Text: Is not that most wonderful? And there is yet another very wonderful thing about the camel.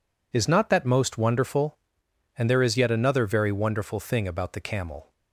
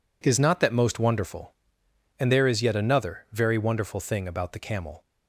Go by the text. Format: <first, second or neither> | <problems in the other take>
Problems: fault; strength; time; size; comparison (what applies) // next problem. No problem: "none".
neither | none